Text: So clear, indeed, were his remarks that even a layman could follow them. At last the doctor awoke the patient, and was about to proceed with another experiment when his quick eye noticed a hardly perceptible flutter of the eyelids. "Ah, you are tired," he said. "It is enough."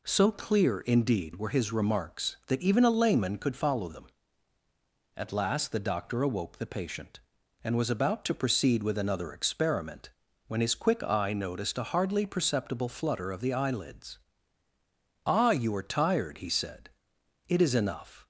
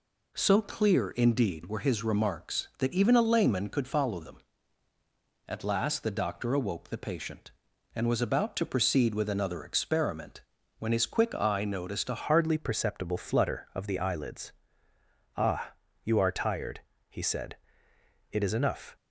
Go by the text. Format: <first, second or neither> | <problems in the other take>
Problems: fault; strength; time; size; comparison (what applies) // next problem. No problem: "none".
first | pauses between "experiment" and "when"; slight; at 10.4 s; 0.36 s long; slight in the first // changes voice at "hardly"; from 12.1 s on; 6.8 s long